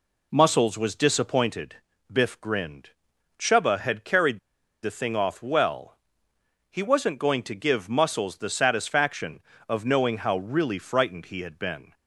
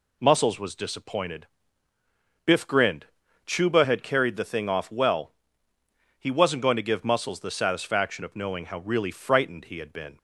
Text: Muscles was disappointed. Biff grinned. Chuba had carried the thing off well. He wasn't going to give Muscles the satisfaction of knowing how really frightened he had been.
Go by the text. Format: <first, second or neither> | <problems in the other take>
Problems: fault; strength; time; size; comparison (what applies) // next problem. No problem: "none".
second | pauses between "carried" and "the"; at 4.3 s; 0.44 s long